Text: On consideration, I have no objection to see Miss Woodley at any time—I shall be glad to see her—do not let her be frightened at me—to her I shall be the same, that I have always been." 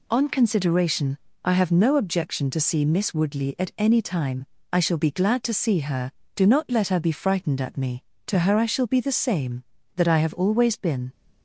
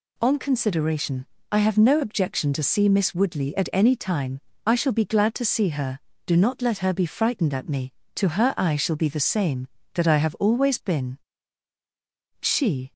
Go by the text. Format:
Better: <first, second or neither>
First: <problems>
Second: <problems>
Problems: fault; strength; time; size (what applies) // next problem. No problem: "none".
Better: first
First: none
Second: goes on to say "She"; from 12.4 s on; 0.52 s long